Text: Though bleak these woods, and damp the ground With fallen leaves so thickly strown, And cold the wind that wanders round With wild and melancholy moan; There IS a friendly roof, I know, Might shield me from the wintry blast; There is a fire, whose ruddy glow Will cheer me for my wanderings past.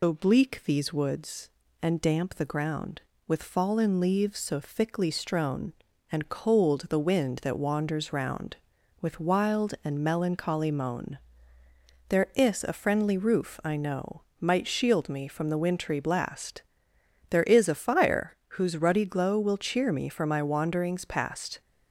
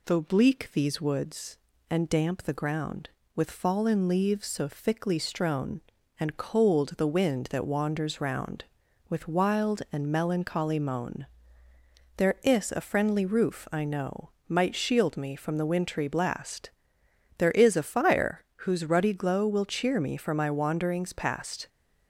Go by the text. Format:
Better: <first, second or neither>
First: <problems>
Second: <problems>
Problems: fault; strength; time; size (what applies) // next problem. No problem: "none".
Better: second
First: loses the start of "Though"; at 0.0 s; 40 ms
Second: none